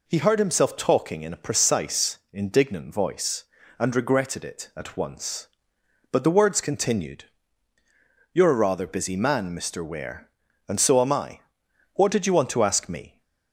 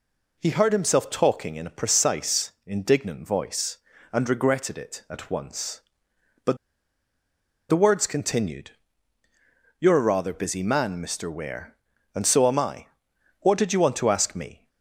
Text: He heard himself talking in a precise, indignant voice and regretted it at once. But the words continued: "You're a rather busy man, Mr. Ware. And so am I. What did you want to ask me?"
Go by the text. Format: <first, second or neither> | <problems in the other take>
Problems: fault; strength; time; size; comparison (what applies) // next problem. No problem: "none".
first | pauses between "But" and "the"; at 6.5 s; 1.1 s long